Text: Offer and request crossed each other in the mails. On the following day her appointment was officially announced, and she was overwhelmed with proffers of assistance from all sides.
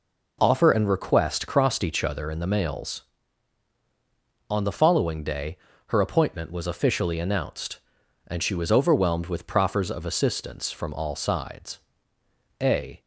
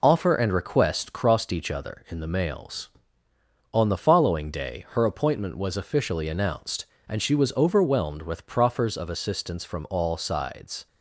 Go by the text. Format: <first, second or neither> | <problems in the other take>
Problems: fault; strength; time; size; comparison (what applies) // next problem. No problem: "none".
second | pauses between "day" and "her"; slight; at 5.5 s; 0.30 s long // goes on to say "A"; slight; from 12.6 s on; 0.40 s long